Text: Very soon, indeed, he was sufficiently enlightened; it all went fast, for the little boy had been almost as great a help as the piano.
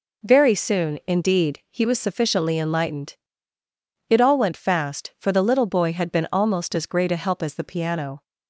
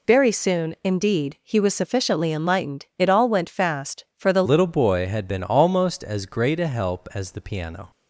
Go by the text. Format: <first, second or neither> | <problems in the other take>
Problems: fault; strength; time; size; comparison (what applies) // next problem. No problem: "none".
first | changes voice at "little"; from 4.4 s on; 3.5 s long